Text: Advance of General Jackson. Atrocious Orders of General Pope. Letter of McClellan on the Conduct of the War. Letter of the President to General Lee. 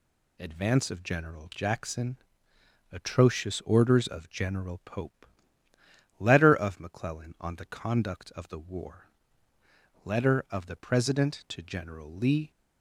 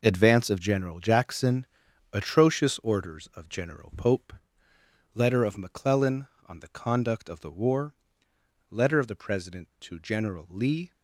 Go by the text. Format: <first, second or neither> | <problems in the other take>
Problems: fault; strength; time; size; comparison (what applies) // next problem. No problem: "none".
neither | none